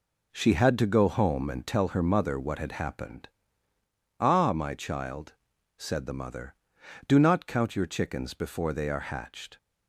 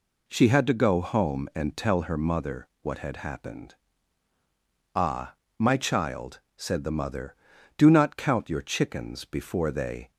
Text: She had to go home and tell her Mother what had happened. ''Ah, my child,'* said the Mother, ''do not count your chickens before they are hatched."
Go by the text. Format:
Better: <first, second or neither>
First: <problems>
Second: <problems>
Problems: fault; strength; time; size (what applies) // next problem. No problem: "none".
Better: first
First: none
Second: pauses between "Mother" and "what"; slight; at 2.6 s; 0.16 s long // stops before "are hatched"; at 10.1 s